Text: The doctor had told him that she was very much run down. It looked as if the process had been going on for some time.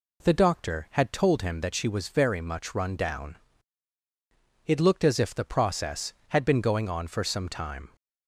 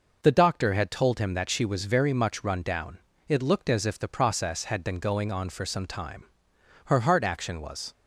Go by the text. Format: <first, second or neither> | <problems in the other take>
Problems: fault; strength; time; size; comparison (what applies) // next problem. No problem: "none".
first | goes on to say "Her heart action was"; noticeable; from 6.8 s on; 1.0 s long